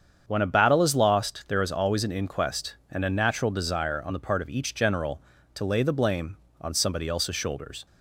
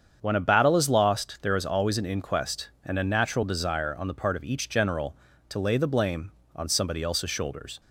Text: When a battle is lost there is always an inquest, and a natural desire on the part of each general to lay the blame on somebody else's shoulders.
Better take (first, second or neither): neither